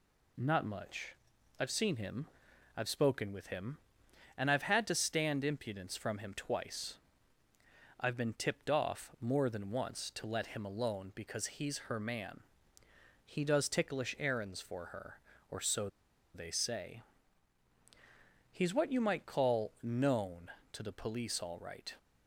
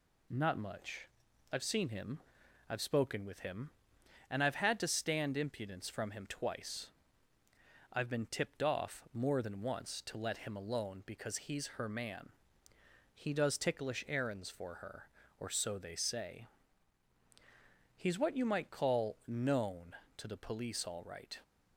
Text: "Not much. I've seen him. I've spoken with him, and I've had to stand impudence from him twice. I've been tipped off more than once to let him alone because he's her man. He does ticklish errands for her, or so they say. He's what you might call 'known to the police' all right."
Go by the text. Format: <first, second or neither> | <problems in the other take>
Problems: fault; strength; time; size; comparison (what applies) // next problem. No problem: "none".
second | pauses between "so" and "they"; noticeable; at 15.8 s; 0.47 s long